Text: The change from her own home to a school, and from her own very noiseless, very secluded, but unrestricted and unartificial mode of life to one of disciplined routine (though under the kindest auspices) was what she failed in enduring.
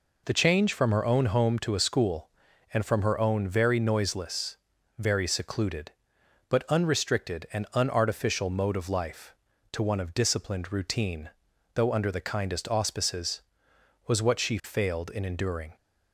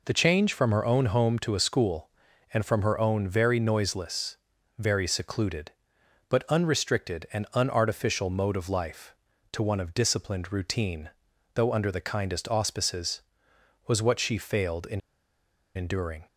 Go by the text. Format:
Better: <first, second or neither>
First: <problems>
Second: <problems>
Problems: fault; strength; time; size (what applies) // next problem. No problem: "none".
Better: first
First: none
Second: pauses between "in" and "enduring"; noticeable; at 14.9 s; 0.75 s long